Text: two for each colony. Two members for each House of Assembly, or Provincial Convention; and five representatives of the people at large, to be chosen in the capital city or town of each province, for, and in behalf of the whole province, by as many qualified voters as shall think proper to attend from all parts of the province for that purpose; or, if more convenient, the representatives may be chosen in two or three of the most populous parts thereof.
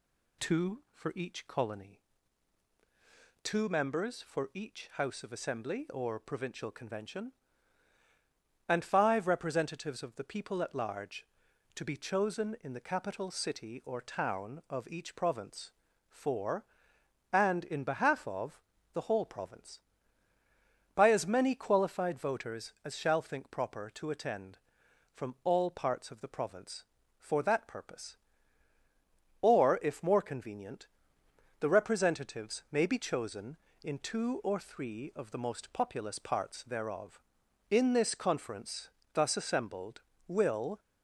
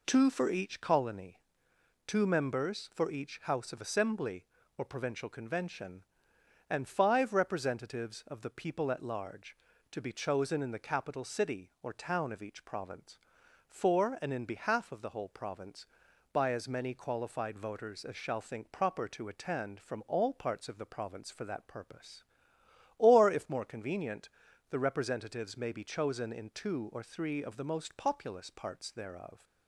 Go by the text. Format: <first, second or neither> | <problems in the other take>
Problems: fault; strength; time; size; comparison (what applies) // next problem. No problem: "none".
second | pauses between "of" and "the"; slight; at 18.5 s; 0.34 s long // goes on to say "In this conference thus assembled will"; strong; from 37.6 s on; 3.1 s long